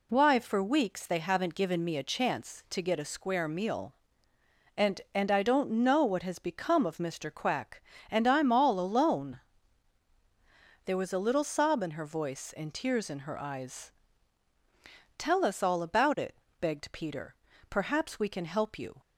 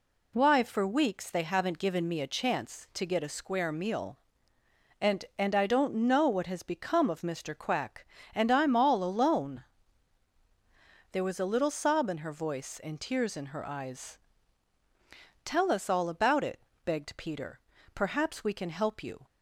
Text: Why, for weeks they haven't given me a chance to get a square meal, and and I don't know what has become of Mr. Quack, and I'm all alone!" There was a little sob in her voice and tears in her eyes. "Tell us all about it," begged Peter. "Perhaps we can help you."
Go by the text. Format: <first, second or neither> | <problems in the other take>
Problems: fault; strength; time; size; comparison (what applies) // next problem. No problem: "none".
neither | none